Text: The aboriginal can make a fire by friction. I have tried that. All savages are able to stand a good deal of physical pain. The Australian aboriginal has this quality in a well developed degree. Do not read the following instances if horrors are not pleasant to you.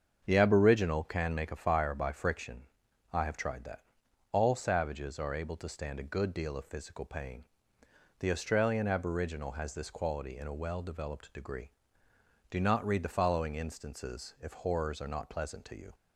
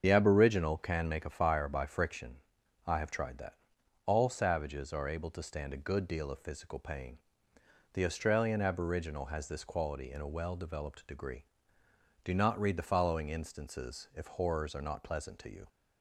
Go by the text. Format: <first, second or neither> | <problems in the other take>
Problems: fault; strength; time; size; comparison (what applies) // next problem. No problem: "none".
first | loses the start of "The"; at 0.0 s; 55 ms // starts louder than the rest; until 1.0 s; 7 dB; also in the first